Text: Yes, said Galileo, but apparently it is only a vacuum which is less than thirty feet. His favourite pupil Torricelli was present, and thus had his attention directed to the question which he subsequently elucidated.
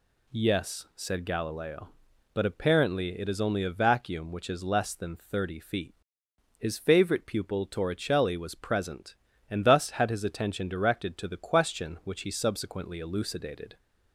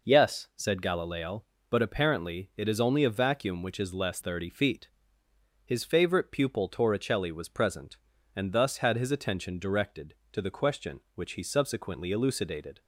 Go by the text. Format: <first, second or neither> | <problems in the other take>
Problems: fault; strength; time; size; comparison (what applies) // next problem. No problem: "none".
first | skips "than"; at 4.1 s